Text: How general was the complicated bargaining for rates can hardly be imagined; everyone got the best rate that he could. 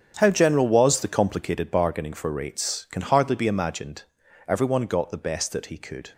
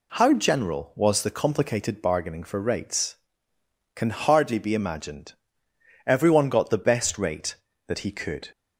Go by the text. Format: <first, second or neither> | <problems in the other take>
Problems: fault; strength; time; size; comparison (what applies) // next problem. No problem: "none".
second | starts louder than the rest; strong; until 1.2 s; 8.5 dB // skips "rate"; at 5.5 s